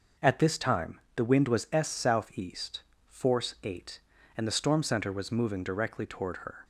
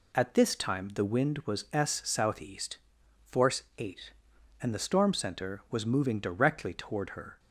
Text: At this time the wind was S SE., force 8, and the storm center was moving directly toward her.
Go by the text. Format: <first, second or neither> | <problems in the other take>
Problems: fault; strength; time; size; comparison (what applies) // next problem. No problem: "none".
neither | none